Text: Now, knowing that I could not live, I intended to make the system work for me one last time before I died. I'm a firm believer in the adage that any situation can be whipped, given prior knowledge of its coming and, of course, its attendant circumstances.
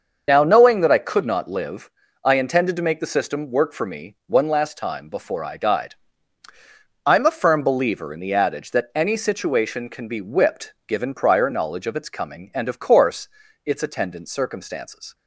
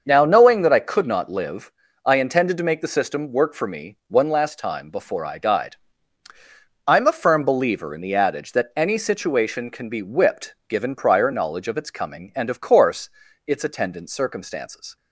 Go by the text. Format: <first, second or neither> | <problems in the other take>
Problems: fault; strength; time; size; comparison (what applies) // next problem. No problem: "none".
second | loses the start of "Now"; at 0.2 s; 30 ms // starts louder than the rest; until 1.2 s; 6.5 dB; also in the second